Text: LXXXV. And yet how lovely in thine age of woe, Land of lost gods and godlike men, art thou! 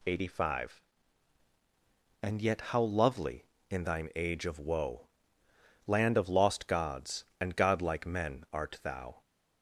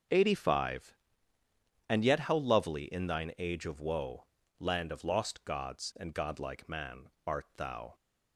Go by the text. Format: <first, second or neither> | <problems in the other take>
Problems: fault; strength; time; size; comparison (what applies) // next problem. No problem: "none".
first | starts louder than the rest; until 2.0 s; 6 dB // says "man" for "men"; at 6.6 s